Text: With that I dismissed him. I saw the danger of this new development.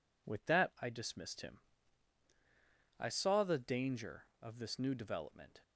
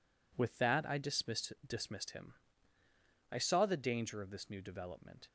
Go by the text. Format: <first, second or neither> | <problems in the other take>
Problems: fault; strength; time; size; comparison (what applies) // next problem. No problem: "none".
first | says "dismissed" twice; at 1.6 s